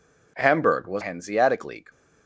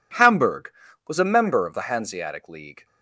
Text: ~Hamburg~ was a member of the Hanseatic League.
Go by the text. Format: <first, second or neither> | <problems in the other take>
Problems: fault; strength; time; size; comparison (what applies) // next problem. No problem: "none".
second | skips "a member of the"; at 1.0 s